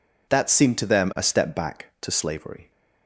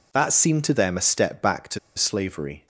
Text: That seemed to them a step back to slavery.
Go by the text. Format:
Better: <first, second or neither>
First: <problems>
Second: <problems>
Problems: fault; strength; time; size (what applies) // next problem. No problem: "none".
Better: first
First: none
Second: pauses between "to" and "slavery"; slight; at 1.7 s; 0.17 s long